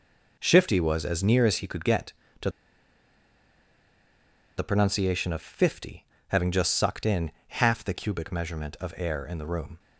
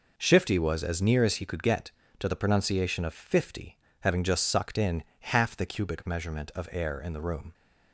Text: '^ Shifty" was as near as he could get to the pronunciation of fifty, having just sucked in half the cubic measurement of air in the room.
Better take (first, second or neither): second